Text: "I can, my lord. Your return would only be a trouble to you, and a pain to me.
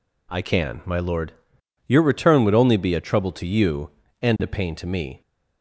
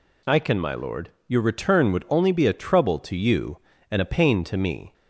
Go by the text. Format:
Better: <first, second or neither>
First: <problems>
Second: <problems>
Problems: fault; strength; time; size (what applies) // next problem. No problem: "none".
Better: neither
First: none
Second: none